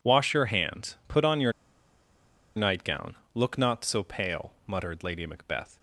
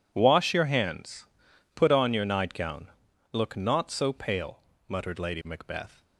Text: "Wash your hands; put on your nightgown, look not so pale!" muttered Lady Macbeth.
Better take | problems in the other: second | pauses between "your" and "nightgown"; at 1.5 s; 1.0 s long

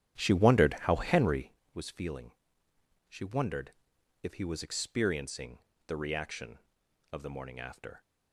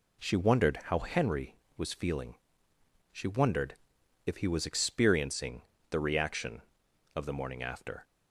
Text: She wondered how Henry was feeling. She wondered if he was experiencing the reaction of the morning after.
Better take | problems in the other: second | starts louder than the rest; strong; until 1.6 s; 10.5 dB // pauses between "wondered" and "if"; noticeable; at 3.7 s; 0.50 s long; noticeable in the second // pauses between "experiencing" and "the"; slight; at 5.5 s; 0.30 s long; slight in the second

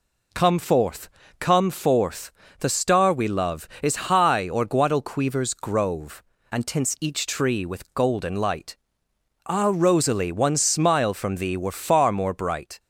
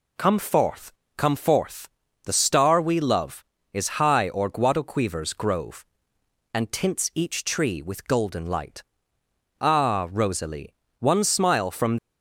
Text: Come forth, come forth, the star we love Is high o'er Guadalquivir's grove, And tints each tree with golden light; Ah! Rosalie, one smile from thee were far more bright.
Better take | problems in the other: first | stops before "thee were far more bright"; at 11.9 s

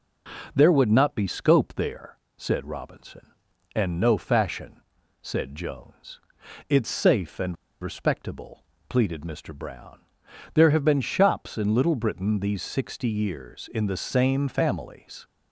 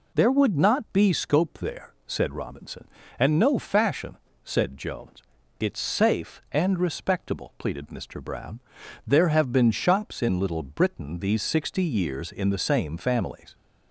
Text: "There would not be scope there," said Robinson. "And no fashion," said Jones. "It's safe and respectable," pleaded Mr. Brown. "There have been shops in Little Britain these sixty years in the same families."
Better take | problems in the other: second | pauses between "and" and "respectable"; slight; at 7.5 s; 0.26 s long

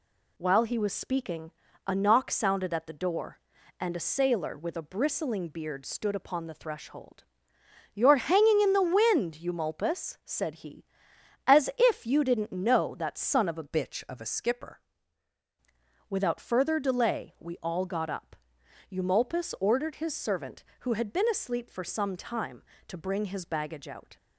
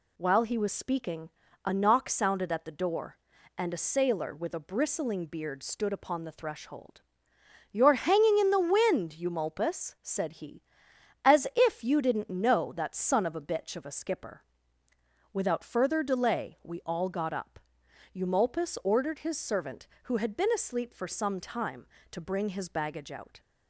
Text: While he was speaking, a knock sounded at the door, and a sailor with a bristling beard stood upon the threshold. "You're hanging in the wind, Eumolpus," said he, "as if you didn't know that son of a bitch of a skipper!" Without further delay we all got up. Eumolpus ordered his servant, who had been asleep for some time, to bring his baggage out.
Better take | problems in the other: second | changes voice from "bitch" to "skipper"; from 13.6 to 14.8 s; 1.2 s long

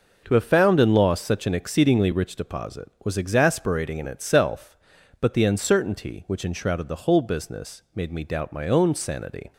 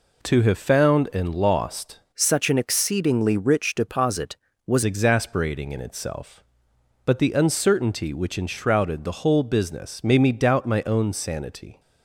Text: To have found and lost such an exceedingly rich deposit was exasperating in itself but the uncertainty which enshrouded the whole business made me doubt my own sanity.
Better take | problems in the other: first | changes voice from "such" to "was"; from 2.1 to 4.8 s; 2.7 s long

